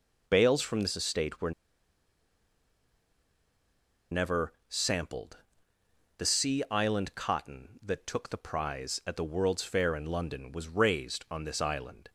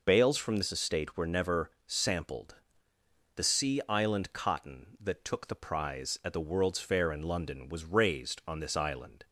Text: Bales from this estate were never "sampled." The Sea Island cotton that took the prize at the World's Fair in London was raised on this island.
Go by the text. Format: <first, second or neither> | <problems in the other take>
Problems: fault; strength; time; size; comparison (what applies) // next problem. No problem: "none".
second | pauses between "were" and "never"; strong; at 1.5 s; 2.5 s long // pauses between "never" and "sampled"; slight; at 4.5 s; 0.16 s long; slight in the second